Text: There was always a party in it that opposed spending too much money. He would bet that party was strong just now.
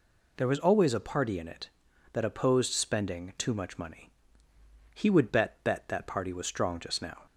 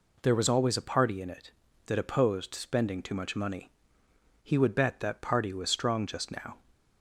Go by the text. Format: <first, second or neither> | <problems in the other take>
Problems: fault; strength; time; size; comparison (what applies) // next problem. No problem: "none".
second | says "bet" twice; at 5.6 s